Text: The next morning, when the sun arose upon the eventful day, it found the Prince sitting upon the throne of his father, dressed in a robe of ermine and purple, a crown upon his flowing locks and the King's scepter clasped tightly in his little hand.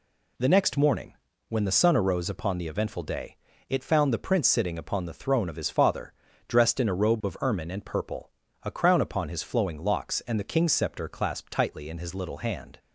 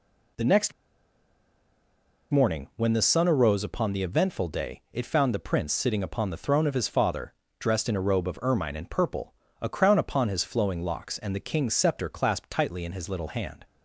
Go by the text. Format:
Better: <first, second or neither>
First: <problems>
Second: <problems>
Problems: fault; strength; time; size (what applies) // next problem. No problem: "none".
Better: first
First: none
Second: pauses between "next" and "morning"; strong; at 0.7 s; 1.5 s long